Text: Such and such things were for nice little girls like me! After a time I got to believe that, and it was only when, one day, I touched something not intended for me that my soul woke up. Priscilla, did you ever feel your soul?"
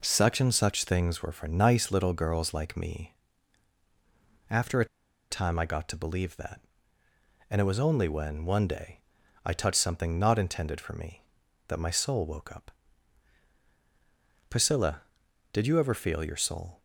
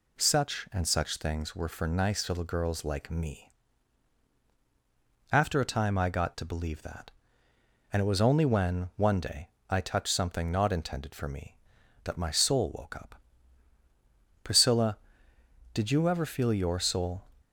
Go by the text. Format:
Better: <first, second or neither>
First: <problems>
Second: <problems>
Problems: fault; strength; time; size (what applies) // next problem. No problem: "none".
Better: second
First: pauses between "a" and "time"; at 4.8 s; 0.45 s long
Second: none